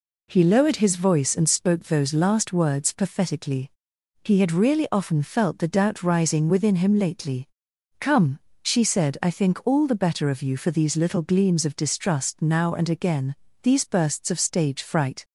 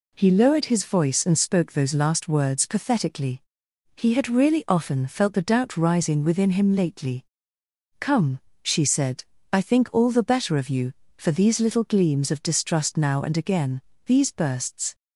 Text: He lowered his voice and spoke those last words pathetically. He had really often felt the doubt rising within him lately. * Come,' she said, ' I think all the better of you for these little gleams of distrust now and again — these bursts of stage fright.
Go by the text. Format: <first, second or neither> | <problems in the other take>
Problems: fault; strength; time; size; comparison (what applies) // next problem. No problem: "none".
first | stops before "of stage fright"; at 14.9 s